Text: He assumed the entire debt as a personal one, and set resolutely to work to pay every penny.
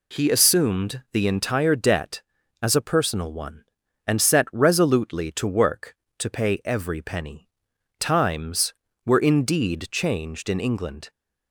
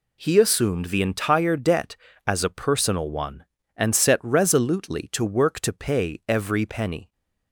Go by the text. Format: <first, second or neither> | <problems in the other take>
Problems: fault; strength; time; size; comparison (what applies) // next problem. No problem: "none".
second | goes on to say "Times were indeed changed in England"; strong; from 7.9 s on; 3.1 s long